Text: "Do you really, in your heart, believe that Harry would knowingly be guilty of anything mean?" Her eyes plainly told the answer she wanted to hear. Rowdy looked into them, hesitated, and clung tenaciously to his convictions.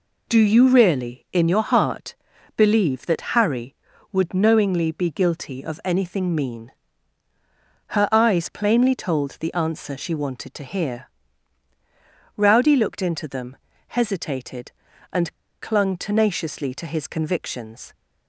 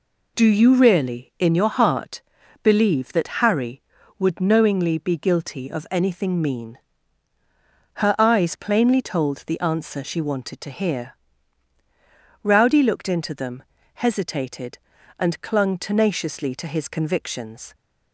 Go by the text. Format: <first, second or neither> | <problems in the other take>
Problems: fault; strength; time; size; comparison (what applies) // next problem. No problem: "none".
second | pauses between "and" and "clung"; slight; at 15.3 s; 0.29 s long